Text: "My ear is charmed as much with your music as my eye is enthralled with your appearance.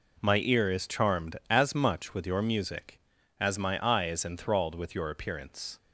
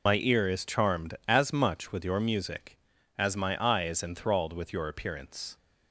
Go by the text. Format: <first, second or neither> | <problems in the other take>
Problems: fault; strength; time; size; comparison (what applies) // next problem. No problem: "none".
first | loses the start of "My"; at 0.0 s; 105 ms